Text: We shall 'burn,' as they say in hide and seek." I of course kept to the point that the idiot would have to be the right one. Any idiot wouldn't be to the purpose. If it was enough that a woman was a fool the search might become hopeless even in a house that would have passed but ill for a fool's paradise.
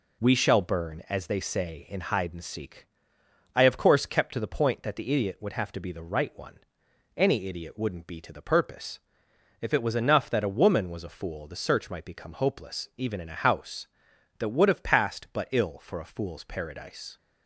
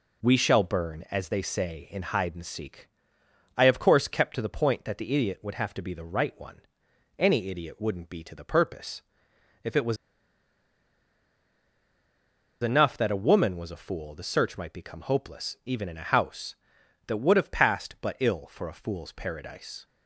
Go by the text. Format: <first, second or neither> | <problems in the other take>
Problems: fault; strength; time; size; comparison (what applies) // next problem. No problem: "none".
first | pauses between "was" and "enough"; strong; at 9.9 s; 2.6 s long